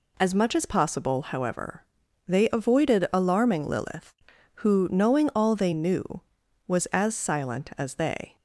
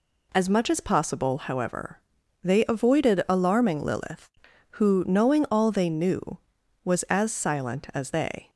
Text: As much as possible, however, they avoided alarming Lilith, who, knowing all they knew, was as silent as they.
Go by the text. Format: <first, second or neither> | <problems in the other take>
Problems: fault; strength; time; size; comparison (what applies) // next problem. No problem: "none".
neither | none